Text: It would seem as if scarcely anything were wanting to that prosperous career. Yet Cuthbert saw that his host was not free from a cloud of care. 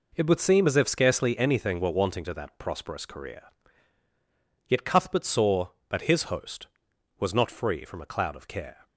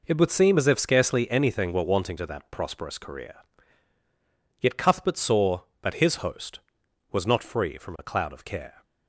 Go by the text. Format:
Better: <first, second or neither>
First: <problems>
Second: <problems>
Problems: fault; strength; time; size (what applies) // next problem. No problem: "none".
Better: neither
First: none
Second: none